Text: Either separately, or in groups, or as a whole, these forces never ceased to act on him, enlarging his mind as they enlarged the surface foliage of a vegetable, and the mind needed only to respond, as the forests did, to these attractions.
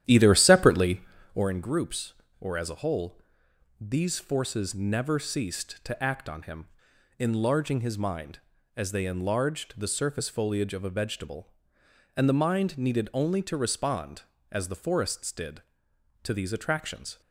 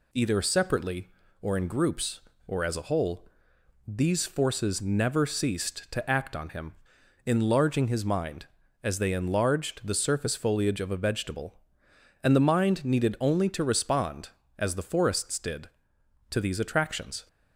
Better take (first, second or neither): second